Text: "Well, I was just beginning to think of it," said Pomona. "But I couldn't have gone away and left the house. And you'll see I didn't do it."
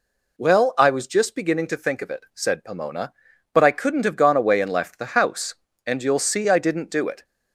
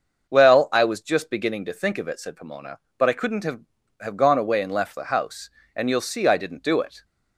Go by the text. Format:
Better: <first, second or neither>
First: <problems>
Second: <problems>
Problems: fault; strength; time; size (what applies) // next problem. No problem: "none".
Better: first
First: none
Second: starts louder than the rest; until 1.3 s; 6.5 dB // says "have" twice; at 4.0 s